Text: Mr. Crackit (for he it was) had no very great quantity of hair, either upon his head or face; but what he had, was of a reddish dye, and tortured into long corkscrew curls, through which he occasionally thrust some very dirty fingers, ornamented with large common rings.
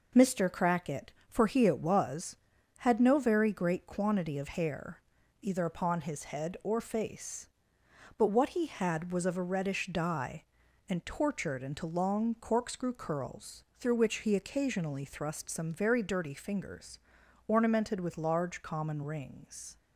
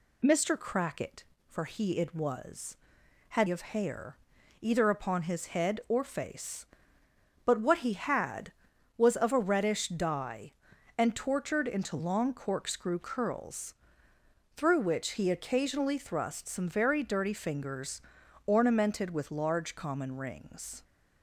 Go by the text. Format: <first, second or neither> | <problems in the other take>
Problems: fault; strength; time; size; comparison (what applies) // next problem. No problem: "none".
first | skips "no very great quantity"; at 3.4 s